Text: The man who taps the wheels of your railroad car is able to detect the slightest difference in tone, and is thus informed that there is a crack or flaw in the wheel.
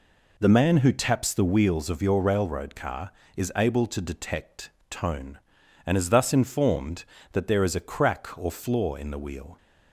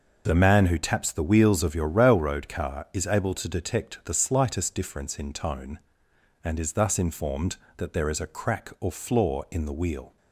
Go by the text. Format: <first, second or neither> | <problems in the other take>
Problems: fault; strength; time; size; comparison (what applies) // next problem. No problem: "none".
second | skips "the slightest difference in"; at 4.7 s